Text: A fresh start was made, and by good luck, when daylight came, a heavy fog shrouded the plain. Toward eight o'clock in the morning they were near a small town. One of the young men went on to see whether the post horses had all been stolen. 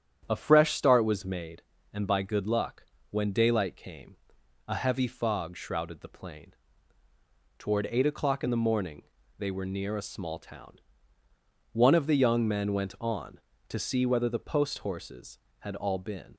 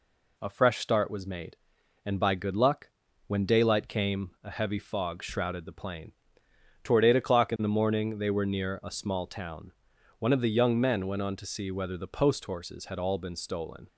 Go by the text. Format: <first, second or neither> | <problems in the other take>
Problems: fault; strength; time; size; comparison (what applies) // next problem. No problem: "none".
second | starts louder than the rest; strong; until 1.3 s; 9 dB // pauses between "morning" and "they"; slight; at 9.0 s; 0.36 s long // stops before "stolen"; at 16.3 s